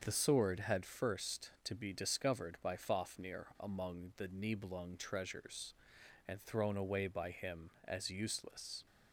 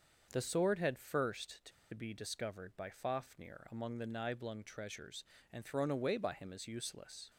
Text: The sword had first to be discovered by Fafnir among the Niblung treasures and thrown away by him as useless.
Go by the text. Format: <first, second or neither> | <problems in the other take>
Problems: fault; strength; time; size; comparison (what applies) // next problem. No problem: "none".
first | starts louder than the rest; until 1.3 s; 6.5 dB; also in the first // pauses between "to" and "be"; slight; at 1.7 s; 0.22 s long